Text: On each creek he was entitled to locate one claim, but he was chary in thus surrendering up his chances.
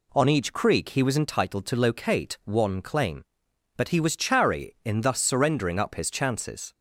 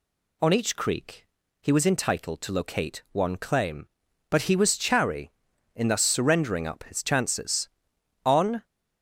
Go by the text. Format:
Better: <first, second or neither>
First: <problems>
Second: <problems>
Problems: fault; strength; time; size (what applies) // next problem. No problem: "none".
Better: first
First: none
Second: pauses between "creek" and "he"; slight; at 1.2 s; 0.34 s long // goes on to say "On"; slight; from 8.2 s on; 0.40 s long